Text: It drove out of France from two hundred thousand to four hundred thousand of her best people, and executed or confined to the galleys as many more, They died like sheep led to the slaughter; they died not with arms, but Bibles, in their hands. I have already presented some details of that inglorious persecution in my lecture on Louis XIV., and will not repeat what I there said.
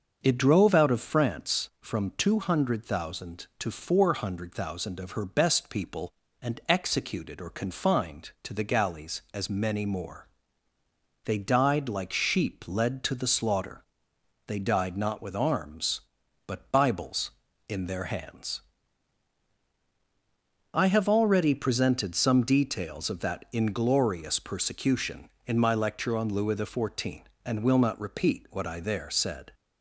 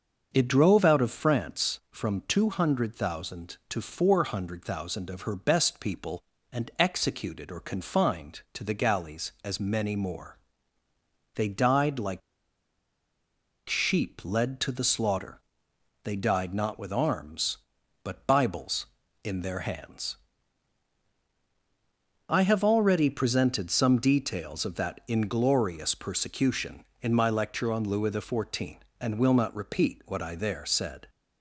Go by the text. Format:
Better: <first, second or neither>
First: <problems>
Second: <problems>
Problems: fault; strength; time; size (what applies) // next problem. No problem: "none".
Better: first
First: starts louder than the rest; until 1.2 s; 6.5 dB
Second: starts louder than the rest; until 1.3 s; 6.5 dB // pauses between "like" and "sheep"; strong; at 12.2 s; 1.4 s long